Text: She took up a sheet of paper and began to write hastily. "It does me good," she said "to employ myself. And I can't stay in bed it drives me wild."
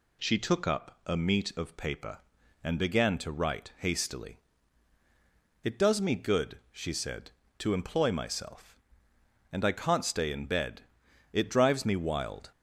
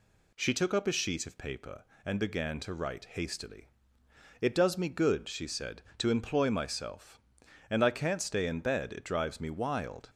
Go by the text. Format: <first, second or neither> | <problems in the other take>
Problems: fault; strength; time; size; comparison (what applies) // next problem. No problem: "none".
second | says "meat" for "sheet"; at 1.1 s // pauses between "bed" and "it"; noticeable; at 10.8 s; 0.50 s long